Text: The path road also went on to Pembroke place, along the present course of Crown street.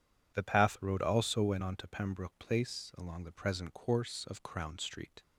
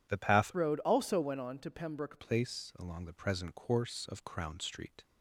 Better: first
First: none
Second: changes voice from "road" to "Pembroke"; from 0.5 to 2.2 s; 1.7 s long

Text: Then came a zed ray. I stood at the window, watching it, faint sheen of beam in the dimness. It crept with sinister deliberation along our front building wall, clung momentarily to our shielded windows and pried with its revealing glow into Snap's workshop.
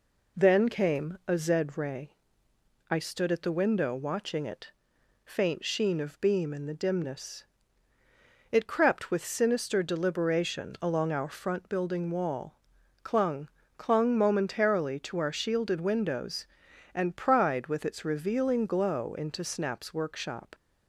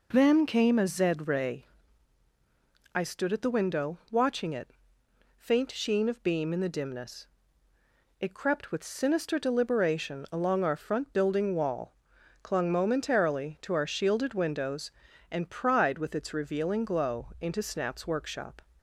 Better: second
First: says "clung" twice; at 13.7 s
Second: none

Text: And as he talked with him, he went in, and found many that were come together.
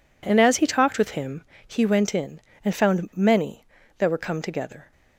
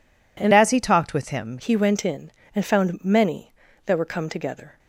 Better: first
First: none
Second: changes voice from "as" to "him"; from 0.5 to 1.5 s; 1.0 s long

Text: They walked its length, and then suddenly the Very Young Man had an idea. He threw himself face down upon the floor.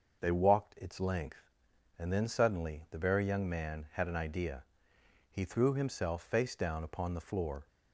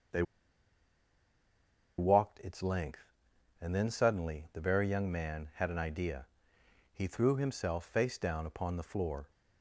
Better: first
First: starts louder than the rest; until 1.2 s; 6 dB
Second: starts louder than the rest; until 2.8 s; 6 dB // pauses between "They" and "walked"; strong; at 0.2 s; 1.7 s long

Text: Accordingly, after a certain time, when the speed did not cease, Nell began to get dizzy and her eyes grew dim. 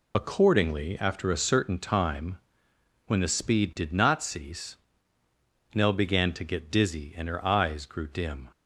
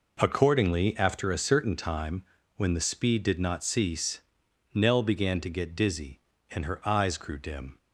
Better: second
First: loses the start of "Accordingly"; at 0.1 s; 45 ms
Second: none

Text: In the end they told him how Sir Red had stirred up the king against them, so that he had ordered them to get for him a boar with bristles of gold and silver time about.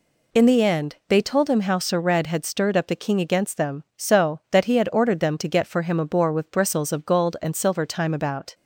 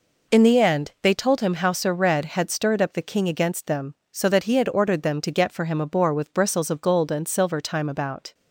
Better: neither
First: none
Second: none

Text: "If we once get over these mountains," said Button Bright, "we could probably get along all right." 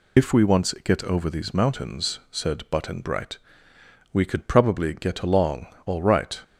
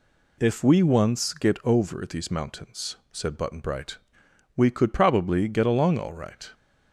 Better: second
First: loses the start of "If"; at 0.1 s; 60 ms // pauses between "along" and "all"; slight; at 5.6 s; 0.18 s long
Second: none

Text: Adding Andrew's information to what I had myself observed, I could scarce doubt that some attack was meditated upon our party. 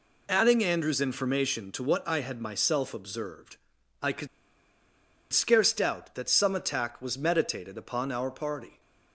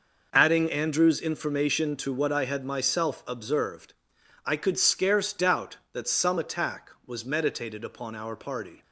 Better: second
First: pauses between "could" and "scarce"; at 4.2 s; 1.0 s long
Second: none

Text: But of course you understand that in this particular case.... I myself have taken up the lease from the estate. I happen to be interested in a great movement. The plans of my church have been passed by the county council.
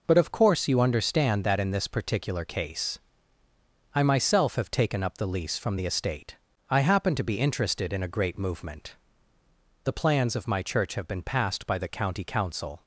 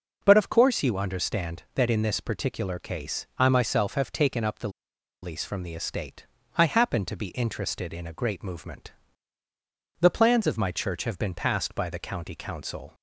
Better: first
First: none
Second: pauses between "the" and "lease"; noticeable; at 4.6 s; 0.53 s long

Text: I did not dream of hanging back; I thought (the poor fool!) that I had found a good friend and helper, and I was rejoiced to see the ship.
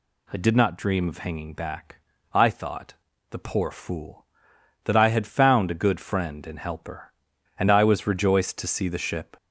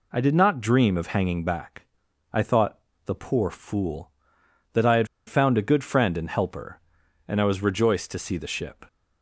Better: first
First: none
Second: pauses between "had" and "found"; slight; at 5.0 s; 0.20 s long

